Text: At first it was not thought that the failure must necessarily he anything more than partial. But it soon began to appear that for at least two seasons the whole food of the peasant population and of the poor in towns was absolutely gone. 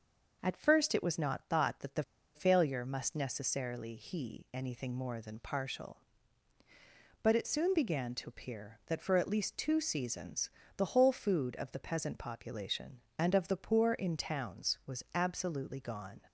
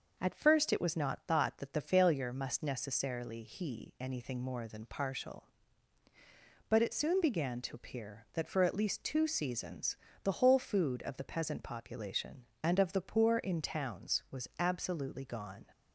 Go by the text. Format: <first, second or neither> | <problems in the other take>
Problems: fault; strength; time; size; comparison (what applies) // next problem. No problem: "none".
second | pauses between "the" and "failure"; slight; at 2.0 s; 0.31 s long // pauses between "seasons" and "the"; slight; at 10.4 s; 0.26 s long; slight in the second